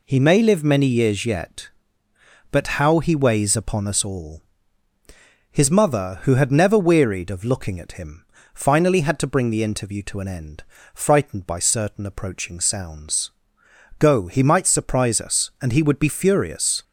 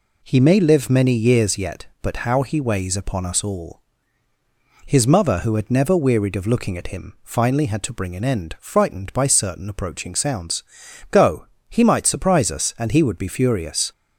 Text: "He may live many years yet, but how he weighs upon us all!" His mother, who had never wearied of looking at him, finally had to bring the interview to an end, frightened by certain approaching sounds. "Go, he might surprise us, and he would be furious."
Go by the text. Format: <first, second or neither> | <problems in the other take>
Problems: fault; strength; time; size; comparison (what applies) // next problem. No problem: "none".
first | skips "the interview to"; at 8.1 s